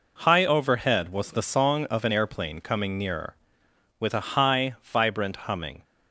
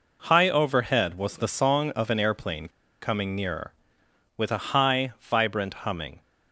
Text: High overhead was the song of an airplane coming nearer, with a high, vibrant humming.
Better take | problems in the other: first | pauses between "airplane" and "coming"; slight; at 2.6 s; 0.32 s long

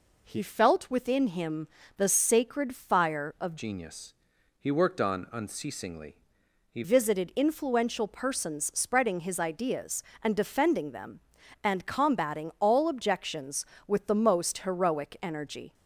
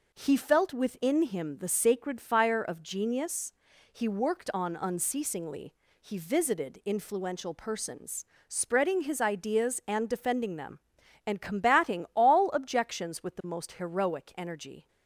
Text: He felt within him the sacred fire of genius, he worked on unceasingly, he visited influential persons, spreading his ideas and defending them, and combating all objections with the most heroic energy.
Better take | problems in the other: second | pauses between "him" and "the"; slight; at 1.6 s; 0.30 s long // changes voice from "genius" to "he"; from 3.5 to 6.8 s; 3.3 s long

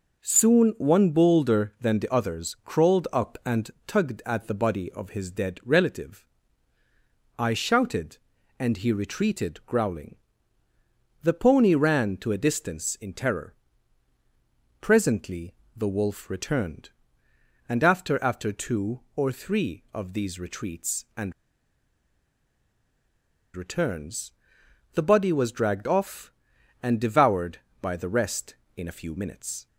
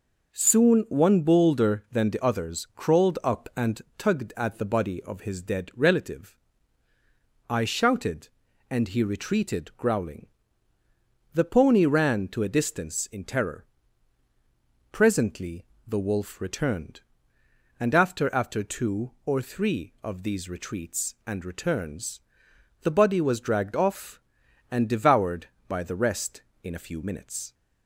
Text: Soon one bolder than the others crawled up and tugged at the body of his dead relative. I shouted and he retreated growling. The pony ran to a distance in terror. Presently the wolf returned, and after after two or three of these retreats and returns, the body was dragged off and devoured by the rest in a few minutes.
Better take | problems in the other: second | pauses between "and" and "tugged"; slight; at 3.6 s; 0.16 s long; slight in the second // pauses between "Presently" and "the"; slight; at 15.5 s; 0.22 s long; slight in the second // pauses between "and" and "returns"; strong; at 21.3 s; 2.2 s long

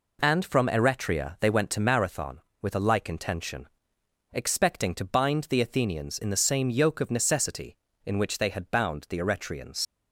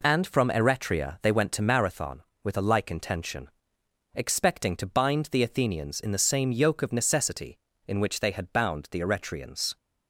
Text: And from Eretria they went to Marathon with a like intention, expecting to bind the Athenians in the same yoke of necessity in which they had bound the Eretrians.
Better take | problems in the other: second | leaves "Eretrians" unfinished; at 9.8 s; 90 ms

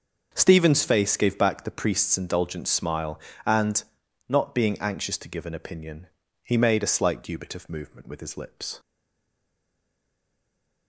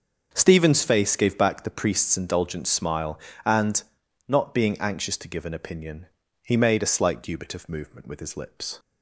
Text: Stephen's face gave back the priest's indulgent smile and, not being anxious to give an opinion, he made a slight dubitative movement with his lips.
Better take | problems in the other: second | starts louder than the rest; until 1.3 s; 6.5 dB; also in the second // stays silent after the last word; noticeable; from 8.7 s on; 2.1 s long

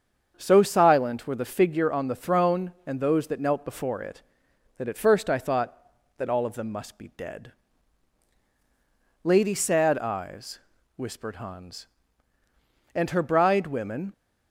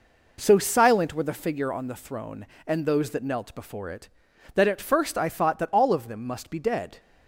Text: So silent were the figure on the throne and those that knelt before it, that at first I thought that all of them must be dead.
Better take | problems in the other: second | starts louder than the rest; strong; until 1.3 s; 7 dB // goes on to say "Lady Sad Eyes whispered Hans and her bride women"; strong; from 9.2 s on; 4.9 s long

